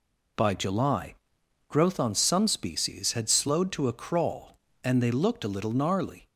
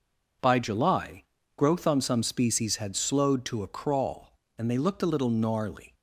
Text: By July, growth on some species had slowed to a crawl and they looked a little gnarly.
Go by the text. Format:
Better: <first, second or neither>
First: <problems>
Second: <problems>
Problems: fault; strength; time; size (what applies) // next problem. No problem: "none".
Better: neither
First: none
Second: none